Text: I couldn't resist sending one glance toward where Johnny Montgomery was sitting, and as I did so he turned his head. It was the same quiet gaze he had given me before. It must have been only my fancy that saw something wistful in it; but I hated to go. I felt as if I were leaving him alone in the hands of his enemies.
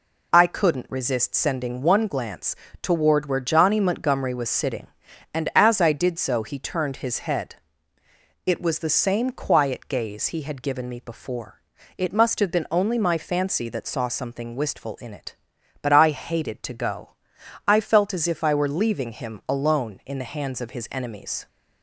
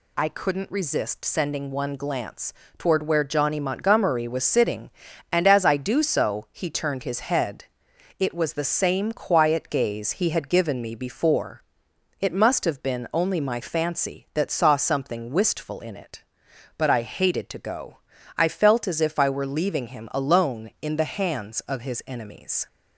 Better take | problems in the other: first | pauses between "glance" and "toward"; slight; at 2.5 s; 0.24 s long; slight in the first // says "do" for "did"; at 5.7 s

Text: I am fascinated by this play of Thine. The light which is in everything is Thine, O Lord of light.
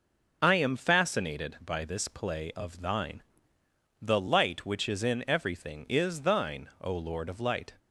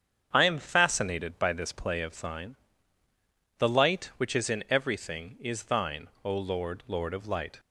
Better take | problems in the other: first | starts louder than the rest; strong; until 1.3 s; 8 dB // says "Lord" twice; at 6.8 s

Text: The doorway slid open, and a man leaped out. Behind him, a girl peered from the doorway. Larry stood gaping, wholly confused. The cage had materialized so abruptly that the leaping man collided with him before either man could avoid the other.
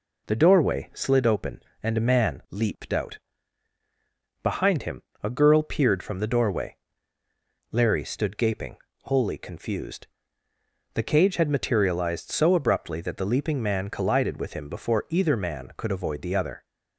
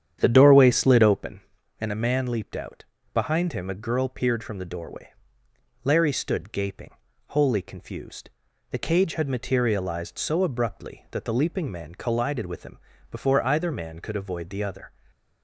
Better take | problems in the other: first | starts louder than the rest; strong; until 1.3 s; 9 dB // pauses between "him" and "before"; slight; at 12.7 s; 0.34 s long // stays silent after the last word; slight; from 14.8 s on; 0.6 s long

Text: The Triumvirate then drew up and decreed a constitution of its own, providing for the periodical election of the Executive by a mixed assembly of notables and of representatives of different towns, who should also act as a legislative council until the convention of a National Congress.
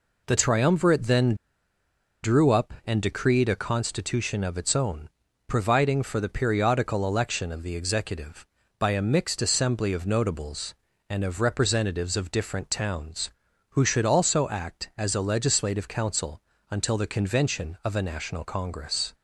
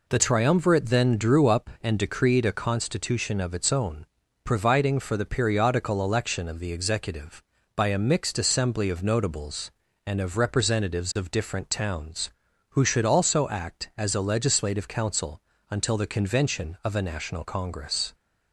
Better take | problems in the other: second | pauses between "then" and "drew"; noticeable; at 1.3 s; 0.89 s long // pauses between "council" and "until"; slight; at 16.4 s; 0.30 s long; slight in the second

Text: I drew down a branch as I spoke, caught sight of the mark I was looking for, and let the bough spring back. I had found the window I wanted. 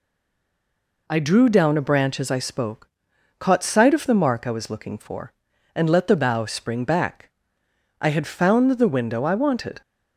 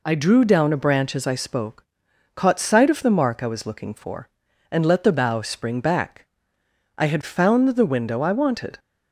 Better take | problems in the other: second | stays silent before the first word; until 1.0 s; 1.0 s long

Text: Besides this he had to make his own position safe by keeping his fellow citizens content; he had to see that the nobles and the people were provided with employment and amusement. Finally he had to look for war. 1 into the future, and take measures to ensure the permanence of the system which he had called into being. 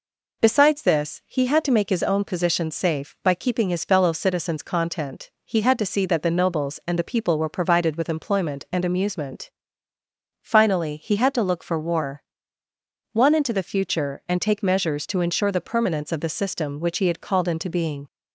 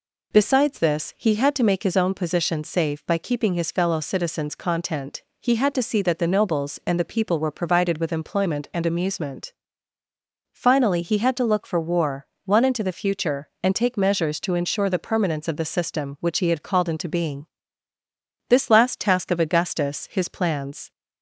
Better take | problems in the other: first | goes on to say "This last task of Augustus his plans"; strong; from 18.4 s on; 2.4 s long

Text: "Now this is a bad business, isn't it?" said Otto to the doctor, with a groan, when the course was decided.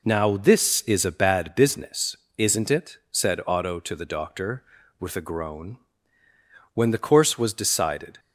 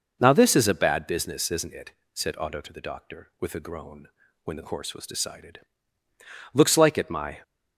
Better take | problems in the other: first | goes on to say "Looks like it my"; noticeable; from 6.5 s on; 0.88 s long

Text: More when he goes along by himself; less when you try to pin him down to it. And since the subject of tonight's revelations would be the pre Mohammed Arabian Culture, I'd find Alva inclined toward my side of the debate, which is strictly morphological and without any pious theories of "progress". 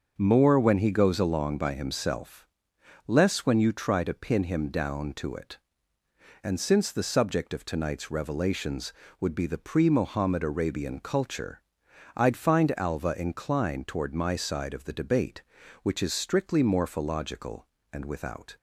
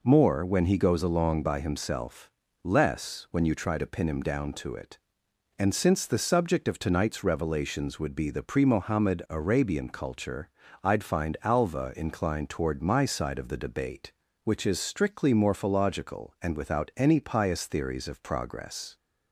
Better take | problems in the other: second | starts louder than the rest; until 1.1 s; 6.5 dB // stops before "any pious theories of progress"; at 18.5 s

